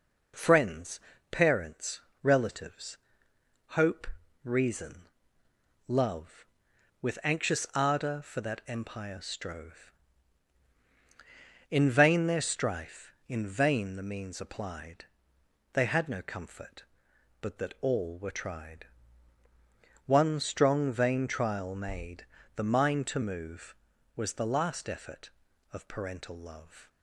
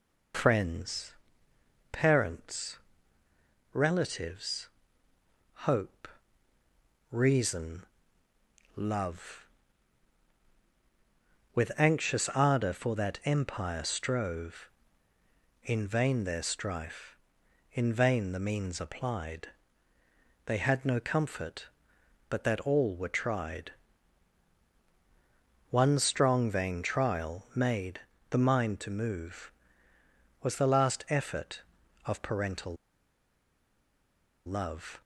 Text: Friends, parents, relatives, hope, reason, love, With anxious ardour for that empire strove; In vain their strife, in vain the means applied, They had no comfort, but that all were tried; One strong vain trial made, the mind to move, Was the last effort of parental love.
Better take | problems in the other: first | pauses between "parental" and "love"; strong; at 32.7 s; 1.7 s long

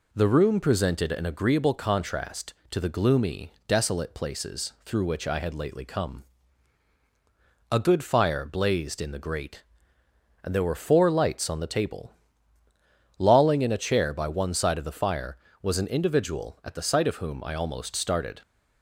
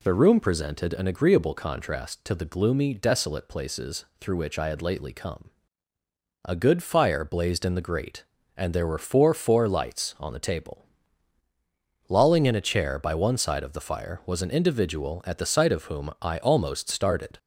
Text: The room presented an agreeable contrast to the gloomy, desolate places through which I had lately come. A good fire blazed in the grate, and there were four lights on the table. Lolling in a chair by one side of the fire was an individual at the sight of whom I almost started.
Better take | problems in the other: first | pauses between "places" and "through"; slight; at 4.0 s; 0.16 s long // says "four" twice; at 9.3 s

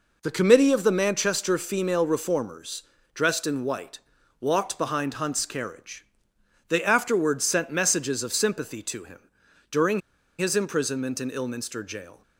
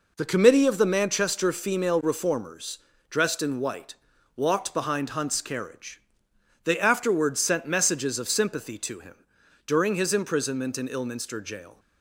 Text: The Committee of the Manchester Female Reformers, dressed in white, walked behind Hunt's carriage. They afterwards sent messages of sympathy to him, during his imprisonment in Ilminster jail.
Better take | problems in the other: second | pauses between "during" and "his"; at 9.9 s; 0.39 s long

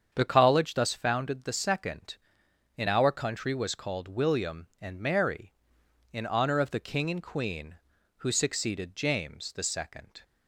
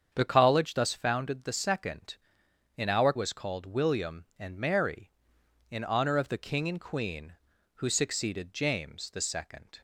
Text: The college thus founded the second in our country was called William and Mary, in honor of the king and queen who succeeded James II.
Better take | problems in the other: first | starts louder than the rest; strong; until 1.1 s; 7.5 dB; strong in the first // skips "country"; at 3.1 s

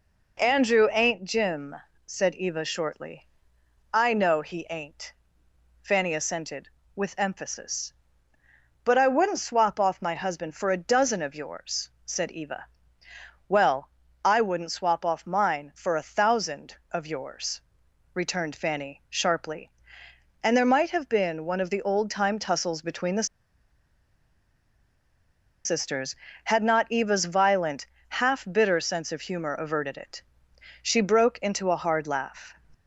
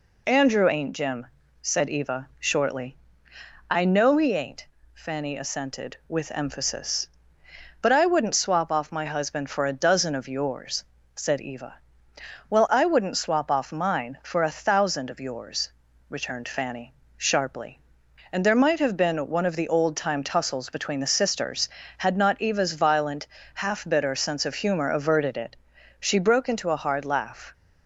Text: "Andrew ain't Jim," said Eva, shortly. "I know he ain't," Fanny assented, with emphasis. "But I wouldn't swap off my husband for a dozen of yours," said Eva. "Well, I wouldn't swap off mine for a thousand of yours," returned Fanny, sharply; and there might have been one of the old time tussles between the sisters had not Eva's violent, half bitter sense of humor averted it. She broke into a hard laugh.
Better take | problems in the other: second | pauses between "the" and "sisters"; strong; at 23.2 s; 2.3 s long

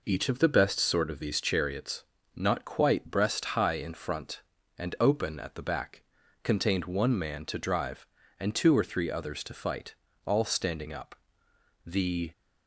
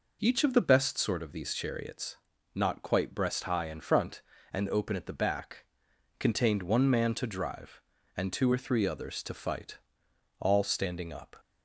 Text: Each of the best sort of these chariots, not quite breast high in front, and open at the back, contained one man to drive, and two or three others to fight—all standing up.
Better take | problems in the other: second | goes on to say "The"; slight; from 11.8 s on; 0.46 s long

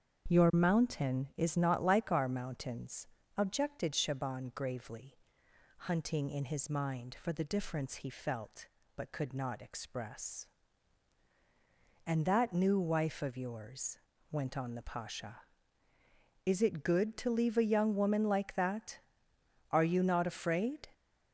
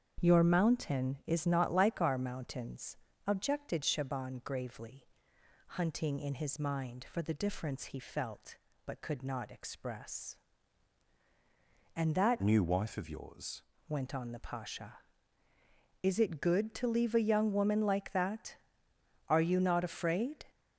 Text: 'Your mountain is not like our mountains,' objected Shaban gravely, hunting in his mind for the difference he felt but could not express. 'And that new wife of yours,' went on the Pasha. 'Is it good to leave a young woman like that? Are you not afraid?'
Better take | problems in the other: first | starts louder than the rest; strong; until 1.2 s; 7.5 dB; strong in the first // changes voice from "new" to "yours"; from 12.4 to 13.6 s; 1.2 s long

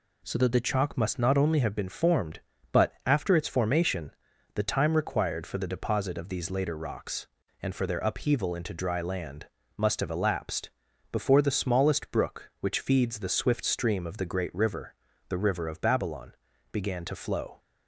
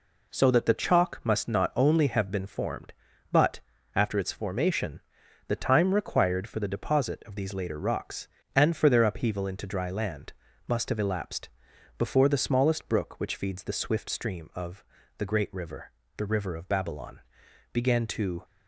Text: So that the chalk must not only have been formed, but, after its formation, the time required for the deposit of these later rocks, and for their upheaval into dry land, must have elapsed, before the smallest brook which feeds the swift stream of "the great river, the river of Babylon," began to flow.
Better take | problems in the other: first | pauses between "of" and "the"; slight; at 14.8 s; 0.34 s long // stops before "flow"; at 18.4 s

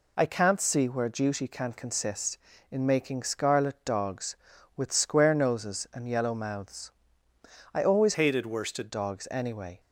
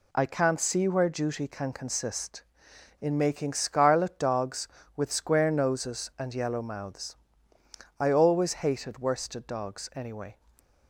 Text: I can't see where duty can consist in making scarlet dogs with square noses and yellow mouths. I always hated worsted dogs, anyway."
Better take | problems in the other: second | changes voice from "hated" to "worsted"; from 8.1 to 8.8 s; 0.7 s long

